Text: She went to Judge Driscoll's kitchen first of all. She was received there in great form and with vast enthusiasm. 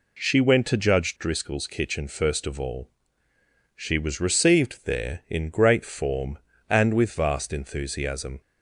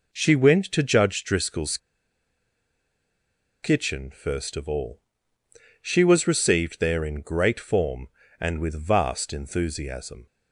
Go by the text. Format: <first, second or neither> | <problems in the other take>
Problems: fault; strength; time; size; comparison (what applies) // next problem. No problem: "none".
first | pauses between "Driscoll's" and "kitchen"; strong; at 1.7 s; 1.8 s long